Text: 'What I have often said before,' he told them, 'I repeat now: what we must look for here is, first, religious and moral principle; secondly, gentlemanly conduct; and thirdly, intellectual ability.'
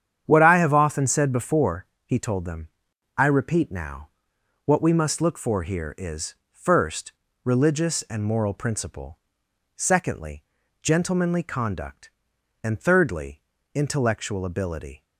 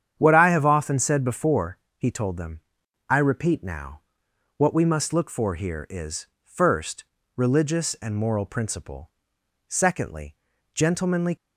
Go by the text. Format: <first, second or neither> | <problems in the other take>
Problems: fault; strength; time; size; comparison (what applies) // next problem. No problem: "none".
first | starts louder than the rest; strong; until 1.2 s; 8.5 dB; strong in the first // stops before "conduct and thirdly intellectual ability"; at 11.3 s